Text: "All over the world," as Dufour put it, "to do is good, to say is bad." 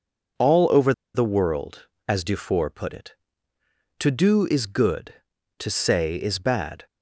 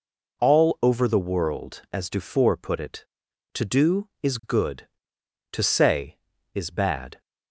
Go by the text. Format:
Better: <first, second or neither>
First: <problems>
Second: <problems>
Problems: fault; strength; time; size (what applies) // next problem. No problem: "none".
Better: second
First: pauses between "over" and "the"; slight; at 0.9 s; 0.22 s long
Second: none